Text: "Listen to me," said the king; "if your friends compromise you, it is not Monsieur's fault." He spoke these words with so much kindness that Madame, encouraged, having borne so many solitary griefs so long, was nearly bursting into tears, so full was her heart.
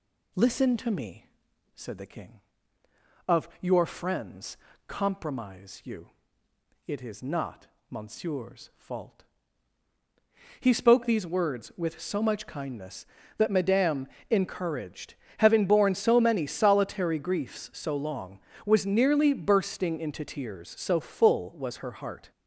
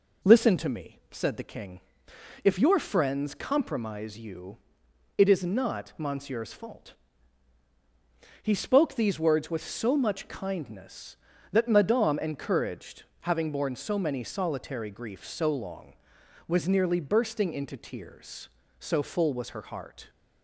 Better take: second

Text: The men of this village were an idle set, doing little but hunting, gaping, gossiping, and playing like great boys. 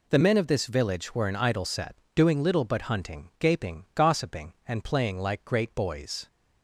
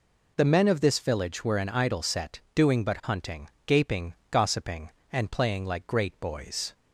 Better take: first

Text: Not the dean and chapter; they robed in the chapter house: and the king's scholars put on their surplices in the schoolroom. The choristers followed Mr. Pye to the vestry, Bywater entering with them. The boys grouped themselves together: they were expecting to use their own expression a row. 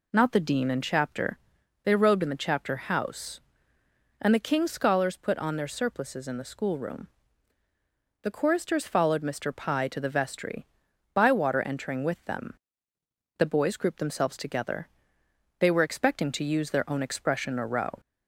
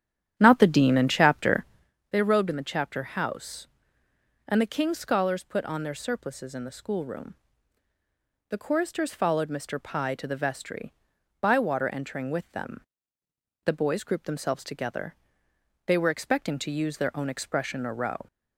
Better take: first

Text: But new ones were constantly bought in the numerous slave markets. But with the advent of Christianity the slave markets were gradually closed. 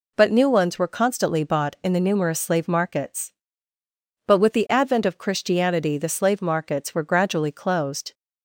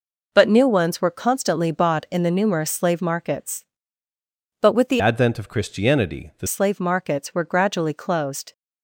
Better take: first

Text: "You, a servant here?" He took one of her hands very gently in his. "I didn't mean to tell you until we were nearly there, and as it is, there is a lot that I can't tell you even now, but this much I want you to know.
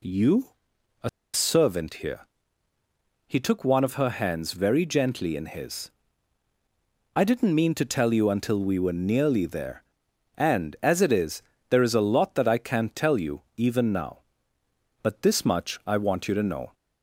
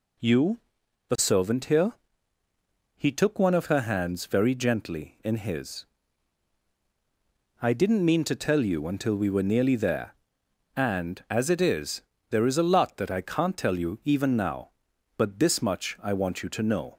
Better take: second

